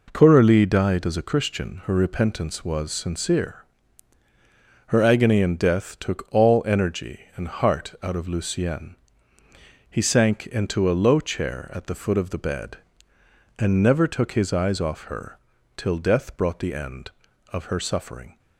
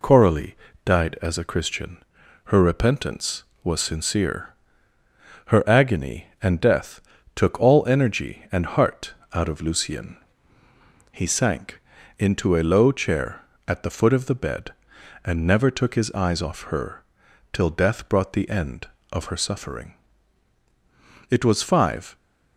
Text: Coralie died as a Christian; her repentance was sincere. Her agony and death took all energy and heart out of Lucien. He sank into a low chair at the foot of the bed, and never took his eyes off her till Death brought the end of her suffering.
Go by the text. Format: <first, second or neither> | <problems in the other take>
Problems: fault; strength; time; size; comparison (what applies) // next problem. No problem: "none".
first | pauses between "Coralie" and "died"; slight; at 0.5 s; 0.28 s long // pauses between "death" and "took"; slight; at 6.9 s; 0.36 s long // pauses between "heart" and "out"; slight; at 9.1 s; 0.18 s long // pauses between "sank" and "into"; at 11.7 s; 0.38 s long // pauses between "her" and "till"; noticeable; at 17.0 s; 0.48 s long; also in the first // goes on to say "It was five"; noticeable; from 21.2 s on; 0.86 s long